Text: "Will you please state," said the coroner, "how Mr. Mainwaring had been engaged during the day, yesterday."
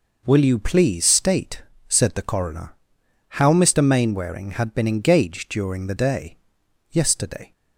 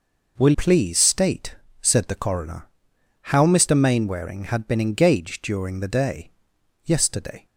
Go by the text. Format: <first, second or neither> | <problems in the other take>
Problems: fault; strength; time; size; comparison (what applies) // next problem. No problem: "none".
first | skips "you"; at 0.5 s